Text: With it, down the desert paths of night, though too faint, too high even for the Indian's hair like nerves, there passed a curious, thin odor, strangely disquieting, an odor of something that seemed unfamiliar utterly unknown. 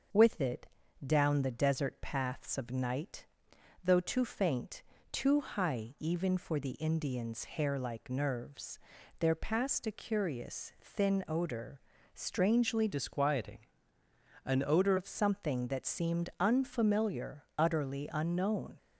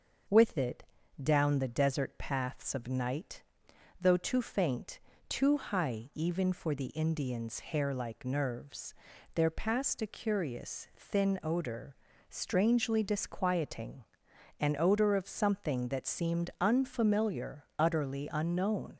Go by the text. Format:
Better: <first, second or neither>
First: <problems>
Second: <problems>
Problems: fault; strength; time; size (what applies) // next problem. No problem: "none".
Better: second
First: starts louder than the rest; until 1.5 s; 6.5 dB // changes voice from "disquieting" to "odor"; from 12.9 to 14.9 s; 2.0 s long // pauses between "unfamiliar" and "utterly"; slight; at 17.4 s; 0.16 s long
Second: starts louder than the rest; until 1.6 s; 6.5 dB // pauses between "unfamiliar" and "utterly"; slight; at 17.6 s; 0.16 s long